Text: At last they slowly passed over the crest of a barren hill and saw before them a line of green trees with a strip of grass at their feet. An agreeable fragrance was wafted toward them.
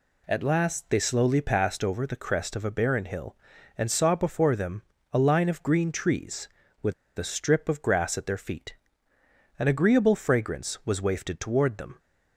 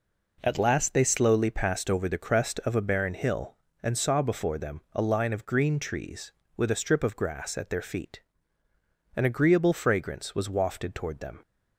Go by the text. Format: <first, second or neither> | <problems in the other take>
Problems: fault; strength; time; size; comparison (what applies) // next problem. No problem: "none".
second | pauses between "them" and "a"; slight; at 4.8 s; 0.30 s long // pauses between "with" and "a"; slight; at 6.9 s; 0.24 s long